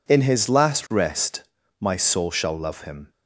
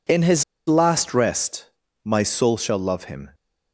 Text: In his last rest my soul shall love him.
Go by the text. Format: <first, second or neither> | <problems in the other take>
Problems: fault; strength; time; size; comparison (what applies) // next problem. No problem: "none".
first | pauses between "his" and "last"; slight; at 0.4 s; 0.25 s long // pauses between "rest" and "my"; at 1.6 s; 0.40 s long; slight in the first